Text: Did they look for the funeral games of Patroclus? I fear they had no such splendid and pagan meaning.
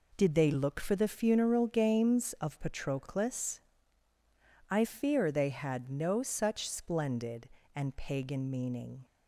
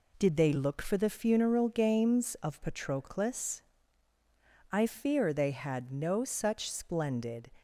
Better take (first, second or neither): first